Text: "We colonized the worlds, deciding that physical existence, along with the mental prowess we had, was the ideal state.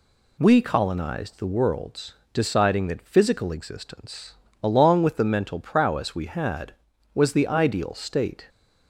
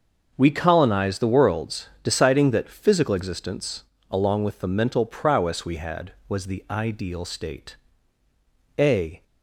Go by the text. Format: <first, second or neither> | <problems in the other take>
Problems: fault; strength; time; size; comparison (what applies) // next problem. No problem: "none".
first | starts louder than the rest; until 1.3 s; 6.5 dB // goes on to say "A"; slight; from 8.7 s on; 0.44 s long